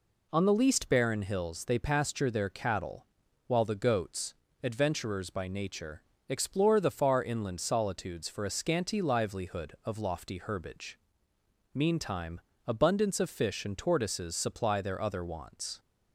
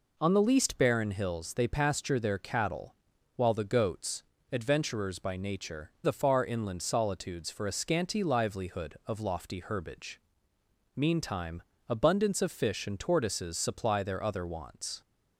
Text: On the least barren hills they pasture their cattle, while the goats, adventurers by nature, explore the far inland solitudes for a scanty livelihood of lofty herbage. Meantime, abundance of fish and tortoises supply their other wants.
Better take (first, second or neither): first